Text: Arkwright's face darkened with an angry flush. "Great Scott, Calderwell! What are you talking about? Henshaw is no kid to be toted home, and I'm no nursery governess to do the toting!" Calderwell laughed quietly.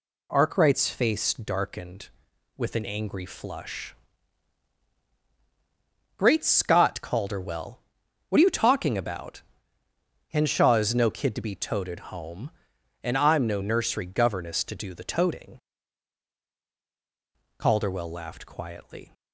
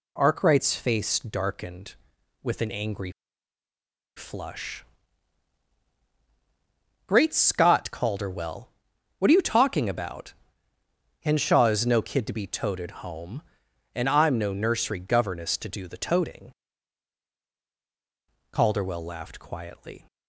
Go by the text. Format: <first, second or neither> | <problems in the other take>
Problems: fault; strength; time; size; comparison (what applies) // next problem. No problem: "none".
first | pauses between "angry" and "flush"; at 3.1 s; 1.0 s long